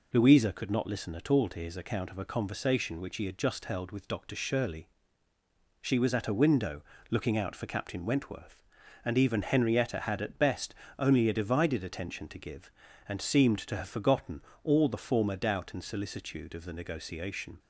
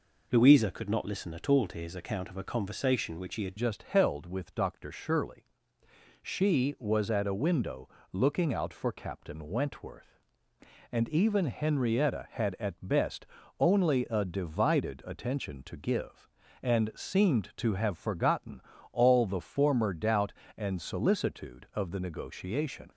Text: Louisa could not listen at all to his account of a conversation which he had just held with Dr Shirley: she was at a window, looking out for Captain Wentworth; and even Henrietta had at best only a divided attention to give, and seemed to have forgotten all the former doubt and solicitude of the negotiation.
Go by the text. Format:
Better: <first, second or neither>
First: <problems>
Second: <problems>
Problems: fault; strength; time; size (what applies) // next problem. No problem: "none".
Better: first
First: pauses between "best" and "only"; slight; at 10.7 s; 0.24 s long // pauses between "forgotten" and "all"; slight; at 14.4 s; 0.22 s long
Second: changes voice at "just"; from 3.5 s on; 19.4 s long // pauses between "best" and "only"; slight; at 13.2 s; 0.34 s long // pauses between "forgotten" and "all"; slight; at 18.6 s; 0.30 s long